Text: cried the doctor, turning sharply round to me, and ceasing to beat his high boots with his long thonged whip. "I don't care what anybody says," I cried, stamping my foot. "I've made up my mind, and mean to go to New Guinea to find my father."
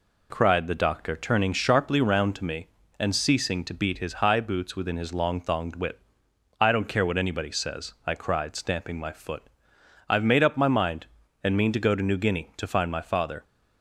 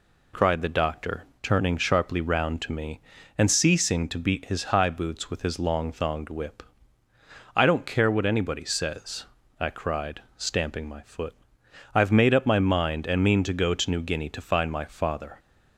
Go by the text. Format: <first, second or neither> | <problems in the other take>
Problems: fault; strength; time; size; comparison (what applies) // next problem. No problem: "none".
second | says "within" for "with"; at 4.7 s